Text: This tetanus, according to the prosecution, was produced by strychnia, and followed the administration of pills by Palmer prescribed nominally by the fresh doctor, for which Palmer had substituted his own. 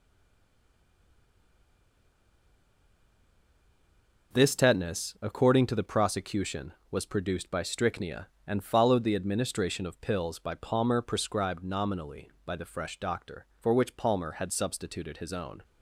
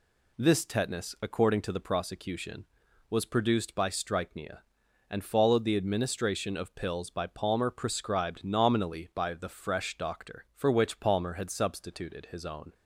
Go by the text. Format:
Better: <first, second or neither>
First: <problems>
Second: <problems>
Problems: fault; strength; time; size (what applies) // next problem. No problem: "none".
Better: second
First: stays silent before the first word; strong; until 4.3 s; 4.3 s long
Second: none